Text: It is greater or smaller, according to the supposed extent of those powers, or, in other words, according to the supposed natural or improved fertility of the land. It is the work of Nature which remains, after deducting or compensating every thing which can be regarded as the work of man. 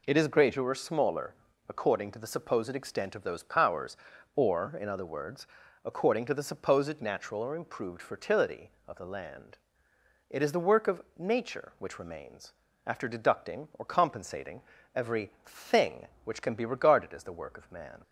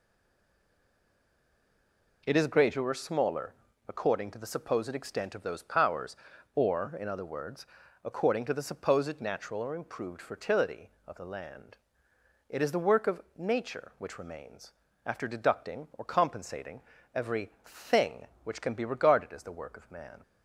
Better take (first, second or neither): first